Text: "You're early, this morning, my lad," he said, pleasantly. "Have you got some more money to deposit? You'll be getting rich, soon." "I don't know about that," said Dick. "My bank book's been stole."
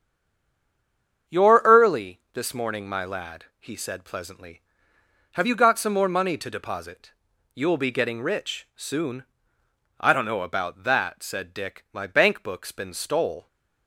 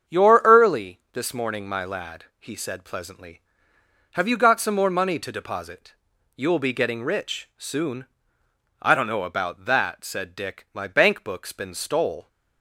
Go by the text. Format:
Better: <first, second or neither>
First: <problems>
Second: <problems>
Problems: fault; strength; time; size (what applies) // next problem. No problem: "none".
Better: second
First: stays silent before the first word; noticeable; until 1.2 s; 1.2 s long // starts louder than the rest; strong; until 2.4 s; 7.5 dB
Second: starts louder than the rest; strong; until 1.2 s; 7.5 dB